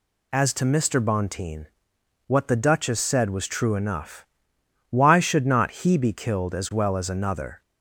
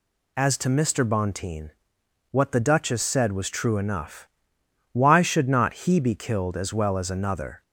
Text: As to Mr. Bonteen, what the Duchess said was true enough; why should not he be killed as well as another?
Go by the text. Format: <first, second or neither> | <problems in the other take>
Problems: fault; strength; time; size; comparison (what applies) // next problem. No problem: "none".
neither | none